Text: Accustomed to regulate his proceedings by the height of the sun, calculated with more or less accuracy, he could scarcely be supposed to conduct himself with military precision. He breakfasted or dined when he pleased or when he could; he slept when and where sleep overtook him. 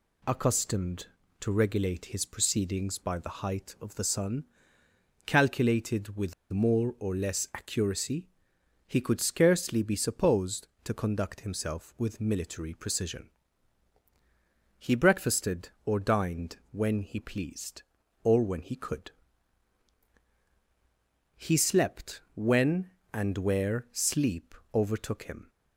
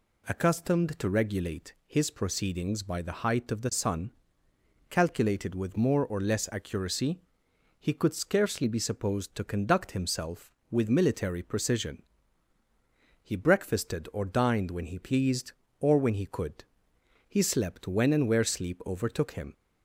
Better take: second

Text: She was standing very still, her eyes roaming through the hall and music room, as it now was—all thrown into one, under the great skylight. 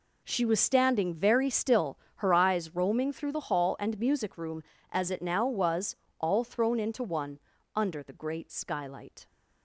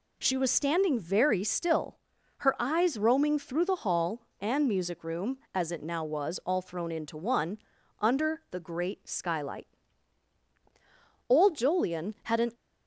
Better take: first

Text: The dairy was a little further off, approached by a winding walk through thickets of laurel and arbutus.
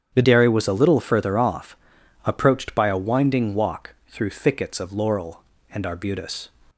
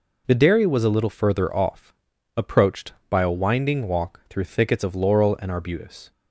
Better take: second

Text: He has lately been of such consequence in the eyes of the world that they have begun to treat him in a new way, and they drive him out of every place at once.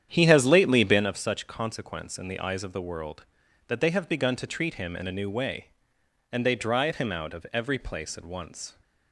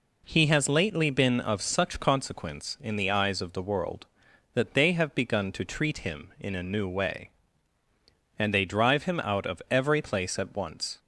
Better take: second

